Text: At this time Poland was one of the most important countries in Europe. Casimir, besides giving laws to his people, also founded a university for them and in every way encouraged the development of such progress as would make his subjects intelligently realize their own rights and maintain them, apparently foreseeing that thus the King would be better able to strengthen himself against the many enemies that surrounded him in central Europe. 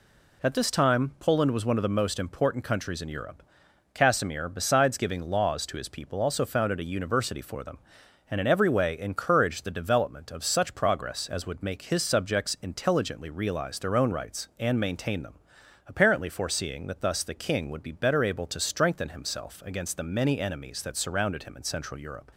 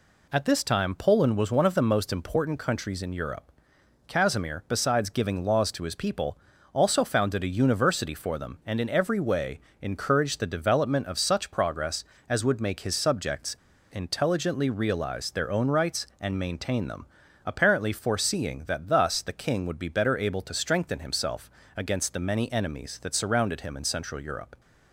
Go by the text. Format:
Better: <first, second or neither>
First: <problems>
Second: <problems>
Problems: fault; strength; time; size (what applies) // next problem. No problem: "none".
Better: first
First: none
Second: pauses between "way" and "encouraged"; slight; at 9.5 s; 0.22 s long // pauses between "subjects" and "intelligently"; at 13.5 s; 0.36 s long // pauses between "himself" and "against"; slight; at 21.4 s; 0.24 s long